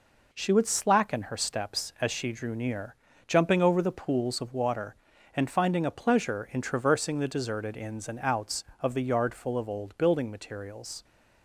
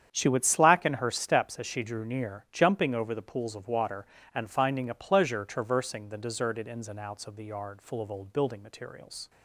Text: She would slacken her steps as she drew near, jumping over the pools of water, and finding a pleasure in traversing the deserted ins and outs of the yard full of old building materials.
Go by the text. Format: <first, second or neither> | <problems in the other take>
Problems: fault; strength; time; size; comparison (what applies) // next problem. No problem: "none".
first | starts louder than the rest; strong; until 1.1 s; 8.5 dB // skips "in"; at 5.4 s